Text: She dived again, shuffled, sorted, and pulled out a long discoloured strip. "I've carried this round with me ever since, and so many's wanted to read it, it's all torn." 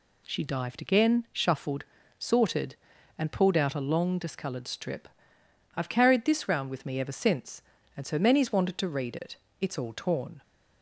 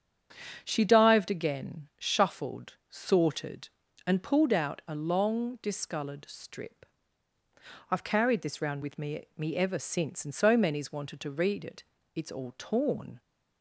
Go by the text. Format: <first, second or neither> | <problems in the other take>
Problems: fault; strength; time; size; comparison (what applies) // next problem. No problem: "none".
first | starts louder than the rest; strong; until 1.6 s; 7.5 dB // says "me" twice; at 9.3 s